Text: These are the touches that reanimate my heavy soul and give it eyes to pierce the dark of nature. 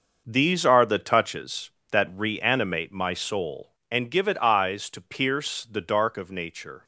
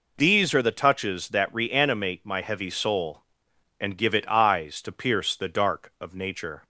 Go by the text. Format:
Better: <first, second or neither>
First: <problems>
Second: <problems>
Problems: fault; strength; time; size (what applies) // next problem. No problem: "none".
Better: second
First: skips "heavy"; at 3.1 s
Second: none